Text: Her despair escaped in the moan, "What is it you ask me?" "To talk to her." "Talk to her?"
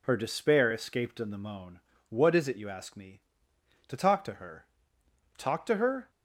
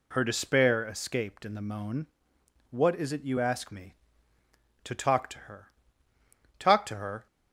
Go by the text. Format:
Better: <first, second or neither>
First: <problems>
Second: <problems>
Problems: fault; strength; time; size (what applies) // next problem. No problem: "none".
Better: neither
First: none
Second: none